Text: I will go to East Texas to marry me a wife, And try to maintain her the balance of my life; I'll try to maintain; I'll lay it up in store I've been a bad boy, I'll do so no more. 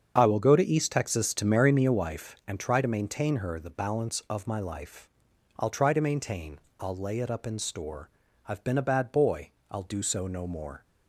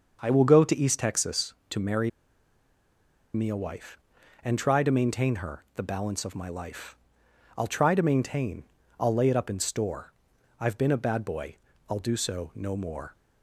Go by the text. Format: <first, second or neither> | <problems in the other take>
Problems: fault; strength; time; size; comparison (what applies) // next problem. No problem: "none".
first | starts louder than the rest; until 1.2 s; 6.5 dB; strong in the first // pauses between "marry" and "me"; at 2.0 s; 1.2 s long // pauses between "store" and "I've"; noticeable; at 10.1 s; 0.48 s long; also in the first